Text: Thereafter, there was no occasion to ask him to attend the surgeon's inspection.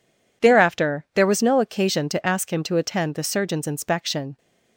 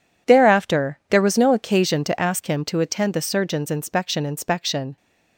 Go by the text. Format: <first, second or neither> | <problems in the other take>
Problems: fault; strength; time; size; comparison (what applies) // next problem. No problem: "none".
first | says "inspection" twice; at 4.2 s